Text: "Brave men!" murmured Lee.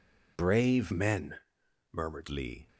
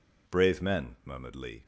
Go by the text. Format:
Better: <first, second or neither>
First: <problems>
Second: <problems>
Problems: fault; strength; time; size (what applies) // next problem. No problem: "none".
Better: second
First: changes voice from "men" to "murmured"; from 0.9 to 2.2 s; 1.3 s long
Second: none